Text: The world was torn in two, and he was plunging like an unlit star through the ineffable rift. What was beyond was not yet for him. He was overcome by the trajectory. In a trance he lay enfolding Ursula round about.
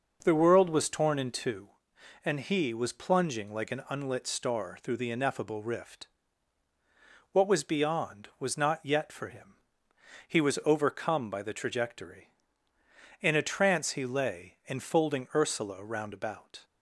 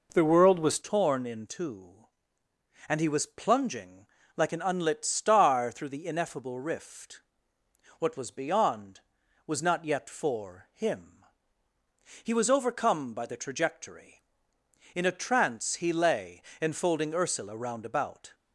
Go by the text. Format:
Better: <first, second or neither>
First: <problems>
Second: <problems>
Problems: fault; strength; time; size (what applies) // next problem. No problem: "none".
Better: first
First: none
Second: changes voice at "torn"; from 0.8 s on; 17.5 s long // pauses between "plunging" and "like"; slight; at 4.0 s; 0.30 s long // pauses between "lay" and "enfolding"; slight; at 16.4 s; 0.20 s long